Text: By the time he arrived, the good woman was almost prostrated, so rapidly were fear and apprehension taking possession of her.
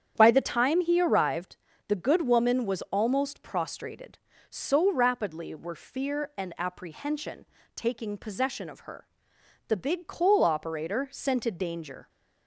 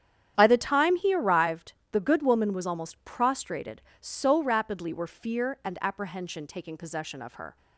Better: second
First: starts louder than the rest; strong; until 1.1 s; 8.5 dB // pauses between "apprehension" and "taking"; slight; at 7.4 s; 0.30 s long // goes on to say "The big coal operator scented danger"; strong; from 9.6 s on; 2.4 s long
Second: starts louder than the rest; strong; until 1.3 s; 9.5 dB

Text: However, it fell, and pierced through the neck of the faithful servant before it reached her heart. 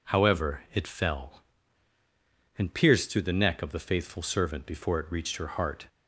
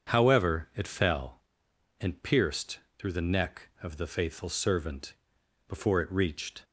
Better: first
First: none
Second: starts louder than the rest; until 1.1 s; 7 dB // pauses between "pierced" and "through"; slight; at 2.7 s; 0.18 s long // pauses between "servant" and "before"; noticeable; at 5.1 s; 0.54 s long // stops before "her heart"; at 6.6 s

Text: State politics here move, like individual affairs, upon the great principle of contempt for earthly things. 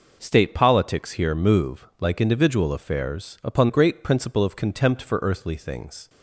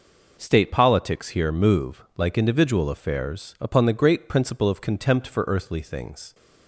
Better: second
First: skips "the"; at 3.6 s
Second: none

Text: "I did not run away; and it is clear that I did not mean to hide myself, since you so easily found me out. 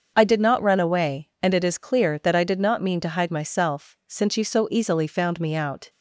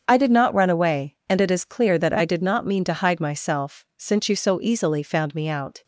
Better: neither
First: starts louder than the rest; until 1.1 s; 7 dB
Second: starts louder than the rest; strong; until 1.1 s; 7 dB

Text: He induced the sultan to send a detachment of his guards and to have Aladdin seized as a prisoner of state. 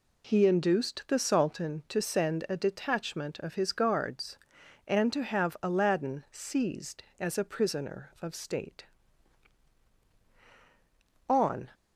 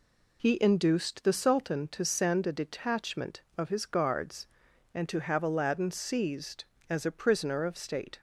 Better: second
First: goes on to say "On"; slight; from 11.2 s on; 0.40 s long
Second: none

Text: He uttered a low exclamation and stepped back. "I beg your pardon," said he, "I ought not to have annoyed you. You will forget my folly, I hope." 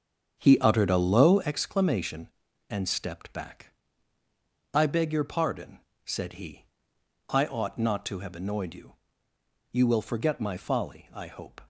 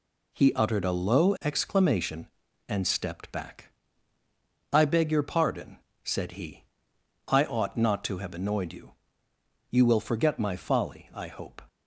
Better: second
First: starts louder than the rest; strong; until 1.5 s; 7.5 dB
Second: none

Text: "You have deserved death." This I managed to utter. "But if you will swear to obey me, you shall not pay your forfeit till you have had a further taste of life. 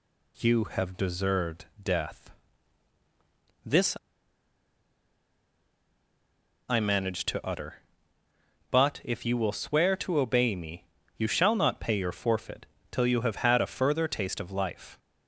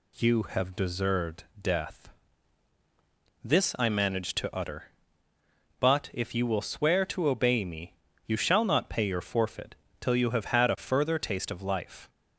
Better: second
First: pauses between "This" and "I"; strong; at 3.9 s; 2.7 s long // pauses between "forfeit" and "till"; slight; at 12.6 s; 0.26 s long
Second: pauses between "forfeit" and "till"; slight; at 9.7 s; 0.26 s long

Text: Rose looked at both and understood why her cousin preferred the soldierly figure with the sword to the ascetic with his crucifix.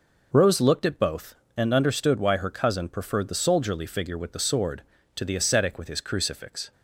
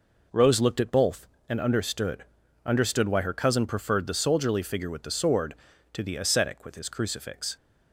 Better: first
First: none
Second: says "understood" twice; at 2.6 s

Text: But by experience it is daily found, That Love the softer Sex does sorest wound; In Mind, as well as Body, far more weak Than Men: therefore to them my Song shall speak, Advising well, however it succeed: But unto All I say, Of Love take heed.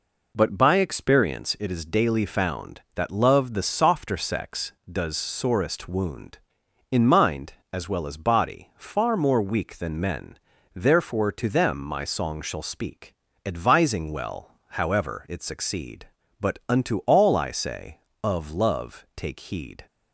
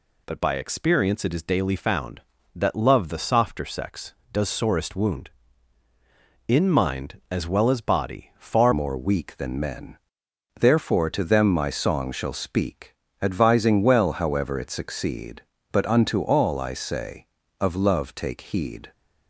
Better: first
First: none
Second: changes voice at "more"; from 8.7 s on; 10.2 s long

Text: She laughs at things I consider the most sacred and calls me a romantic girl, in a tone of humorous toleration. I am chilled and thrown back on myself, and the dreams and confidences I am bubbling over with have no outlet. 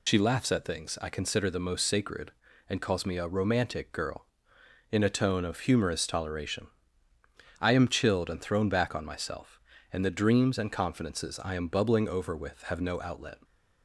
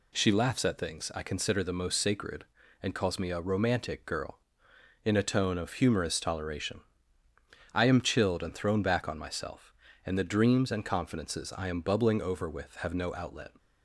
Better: second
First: loses the start of "She"; at 0.0 s; 60 ms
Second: none

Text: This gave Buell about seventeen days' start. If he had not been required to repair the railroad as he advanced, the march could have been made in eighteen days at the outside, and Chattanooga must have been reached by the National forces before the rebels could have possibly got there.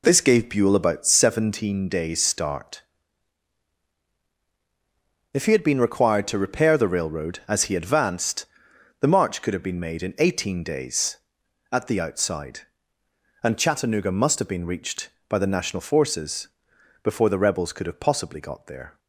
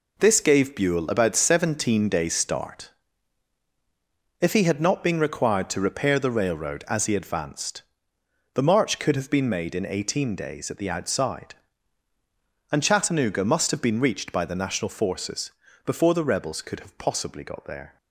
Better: second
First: skips "not"; at 5.6 s // pauses between "forces" and "before"; noticeable; at 16.4 s; 0.54 s long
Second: pauses between "forces" and "before"; slight; at 15.5 s; 0.34 s long

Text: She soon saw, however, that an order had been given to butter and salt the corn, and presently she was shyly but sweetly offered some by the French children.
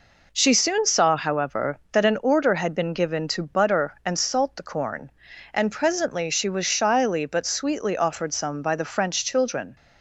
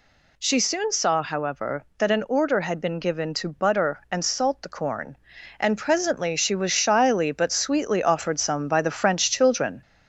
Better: first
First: none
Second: gets louder; throughout; 3.5 dB

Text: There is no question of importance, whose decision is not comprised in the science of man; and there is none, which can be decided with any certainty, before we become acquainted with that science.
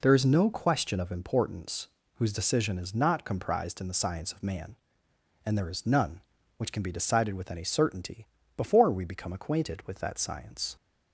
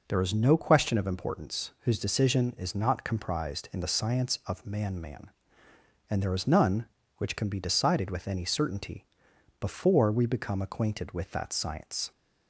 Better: first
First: none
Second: says "man" twice; at 5.0 s

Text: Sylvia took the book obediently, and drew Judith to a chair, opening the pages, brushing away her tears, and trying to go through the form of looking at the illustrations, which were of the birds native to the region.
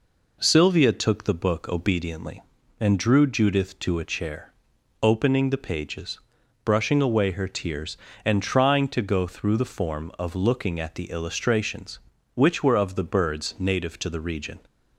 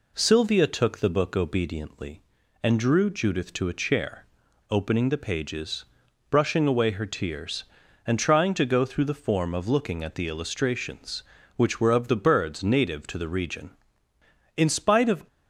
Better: first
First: none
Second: goes on to say "In spite of"; noticeable; from 14.5 s on; 0.70 s long

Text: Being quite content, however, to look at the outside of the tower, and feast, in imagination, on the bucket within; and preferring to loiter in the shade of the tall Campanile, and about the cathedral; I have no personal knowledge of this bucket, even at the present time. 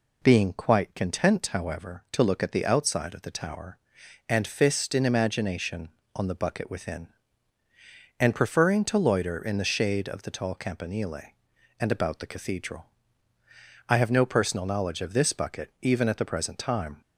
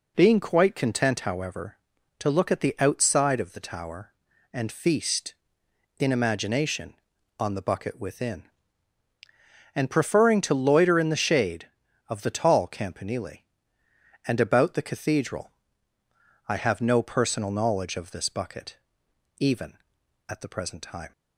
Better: second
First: says "fist" for "feast"; at 4.4 s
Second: none

